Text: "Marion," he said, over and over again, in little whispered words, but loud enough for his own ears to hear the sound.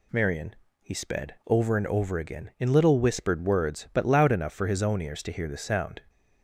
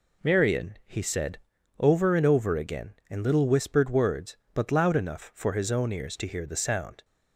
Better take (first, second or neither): second